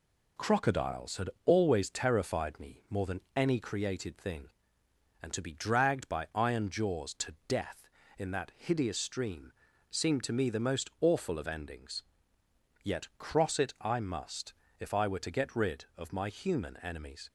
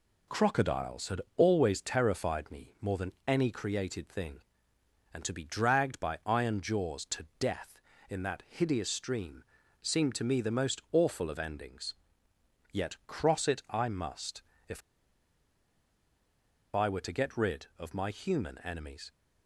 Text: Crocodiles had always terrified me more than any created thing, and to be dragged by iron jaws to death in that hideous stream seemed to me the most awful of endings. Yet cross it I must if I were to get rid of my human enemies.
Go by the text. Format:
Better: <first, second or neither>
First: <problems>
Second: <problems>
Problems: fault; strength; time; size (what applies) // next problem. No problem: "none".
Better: first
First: pauses between "had" and "always"; slight; at 1.2 s; 0.16 s long // pauses between "stream" and "seemed"; at 9.5 s; 0.38 s long // pauses between "must" and "if"; slight; at 14.5 s; 0.24 s long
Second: pauses between "had" and "always"; slight; at 1.2 s; 0.16 s long // pauses between "stream" and "seemed"; at 9.4 s; 0.38 s long // pauses between "must" and "if"; slight; at 14.4 s; 0.24 s long // pauses between "if" and "I"; strong; at 14.8 s; 1.9 s long